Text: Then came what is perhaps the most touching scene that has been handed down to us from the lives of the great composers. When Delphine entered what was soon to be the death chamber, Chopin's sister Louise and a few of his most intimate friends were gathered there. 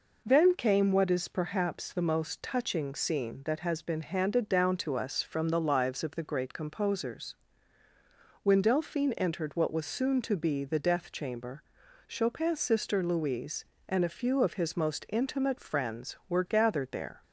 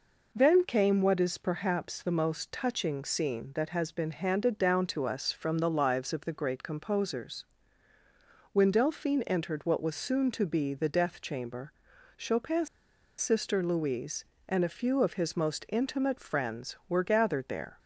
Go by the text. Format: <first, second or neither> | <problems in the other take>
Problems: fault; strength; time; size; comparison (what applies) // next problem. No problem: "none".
first | pauses between "Chopin's" and "sister"; noticeable; at 12.6 s; 0.52 s long